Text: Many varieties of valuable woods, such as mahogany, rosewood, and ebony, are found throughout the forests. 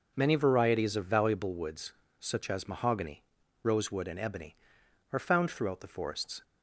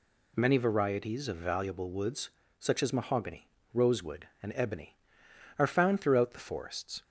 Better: neither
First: none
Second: none

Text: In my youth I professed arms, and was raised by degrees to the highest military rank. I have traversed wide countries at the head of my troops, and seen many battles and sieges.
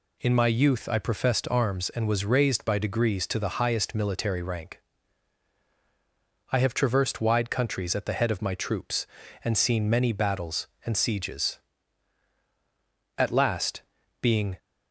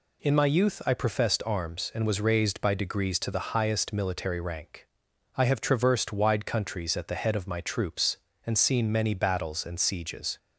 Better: second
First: goes on to say "At last being"; from 13.1 s on; 1.4 s long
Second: none

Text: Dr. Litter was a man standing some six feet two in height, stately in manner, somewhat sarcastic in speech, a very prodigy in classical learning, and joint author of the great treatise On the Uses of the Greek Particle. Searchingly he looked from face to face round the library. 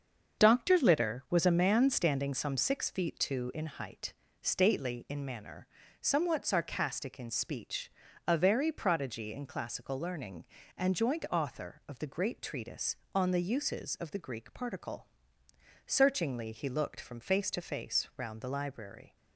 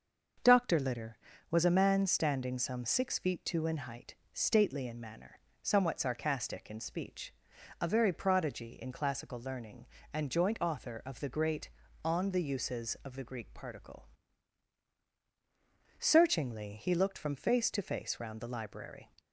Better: first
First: starts louder than the rest; until 1.4 s; 6.5 dB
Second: starts louder than the rest; until 1.7 s; 6.5 dB // skips "treatise"; at 11.8 s

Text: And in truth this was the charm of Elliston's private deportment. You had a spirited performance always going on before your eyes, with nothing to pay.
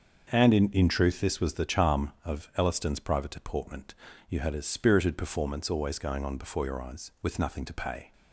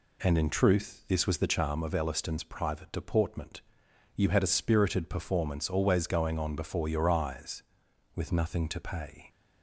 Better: second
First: starts louder than the rest; until 1.3 s; 6.5 dB // says "in" twice; at 0.7 s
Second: none

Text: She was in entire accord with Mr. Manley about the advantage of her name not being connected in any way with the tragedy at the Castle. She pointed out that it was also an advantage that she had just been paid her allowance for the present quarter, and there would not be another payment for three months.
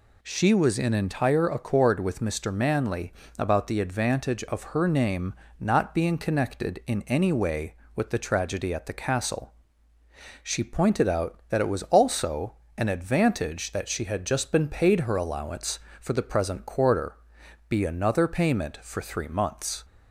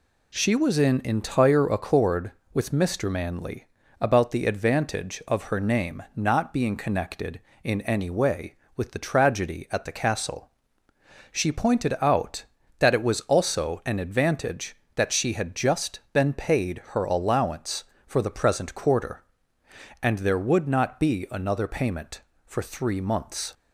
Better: second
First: pauses between "Manley" and "about"; slight; at 3.1 s; 0.28 s long // pauses between "name" and "not"; slight; at 5.3 s; 0.26 s long // pauses between "also" and "an"; slight; at 12.5 s; 0.24 s long // skips "and there would not"; at 17.4 s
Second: pauses between "Manley" and "about"; slight; at 3.6 s; 0.34 s long

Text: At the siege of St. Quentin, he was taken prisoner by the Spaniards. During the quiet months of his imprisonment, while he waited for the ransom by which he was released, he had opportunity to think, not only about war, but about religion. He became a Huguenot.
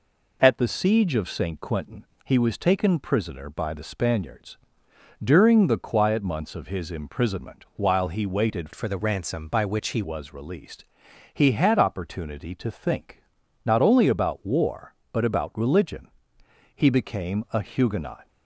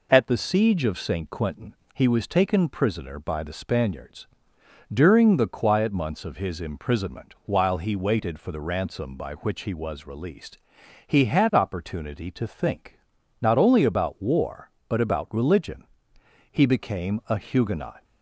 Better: second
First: changes voice from "for" to "he"; from 8.7 to 10.0 s; 1.3 s long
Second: none

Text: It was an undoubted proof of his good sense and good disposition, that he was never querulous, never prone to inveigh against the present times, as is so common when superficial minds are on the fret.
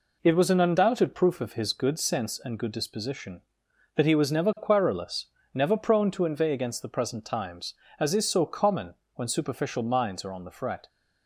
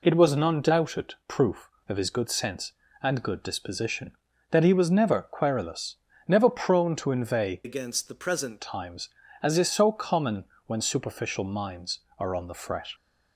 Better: first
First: pauses between "common" and "when"; slight; at 8.9 s; 0.20 s long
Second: changes voice from "against" to "present"; from 7.6 to 8.5 s; 0.9 s long // pauses between "common" and "when"; slight; at 10.4 s; 0.20 s long

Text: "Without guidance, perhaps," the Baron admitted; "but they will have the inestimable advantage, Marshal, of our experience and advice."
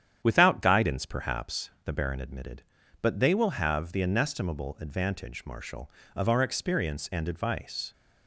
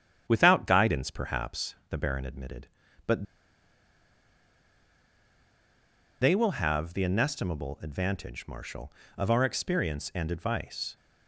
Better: first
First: starts louder than the rest; strong; until 1.2 s; 9.5 dB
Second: starts louder than the rest; strong; until 1.2 s; 9.5 dB // pauses between "but" and "they"; strong; at 3.2 s; 2.9 s long

